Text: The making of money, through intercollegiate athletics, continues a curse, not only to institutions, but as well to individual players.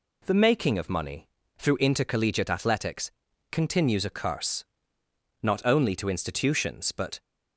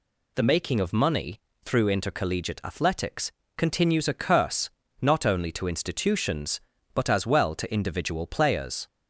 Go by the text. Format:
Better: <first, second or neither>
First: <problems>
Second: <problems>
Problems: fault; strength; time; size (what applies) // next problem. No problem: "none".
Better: second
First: stops before "as well to individual players"; at 7.1 s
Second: none